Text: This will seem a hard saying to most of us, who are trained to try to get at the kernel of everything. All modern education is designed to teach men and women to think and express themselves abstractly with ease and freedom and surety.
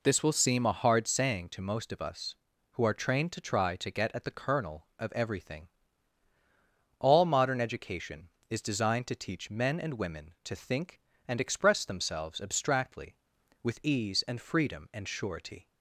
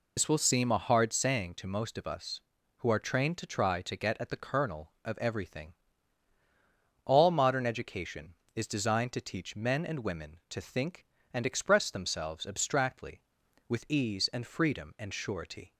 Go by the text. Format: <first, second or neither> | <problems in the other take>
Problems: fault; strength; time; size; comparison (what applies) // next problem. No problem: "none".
first | loses the start of "This"; at 0.1 s; 80 ms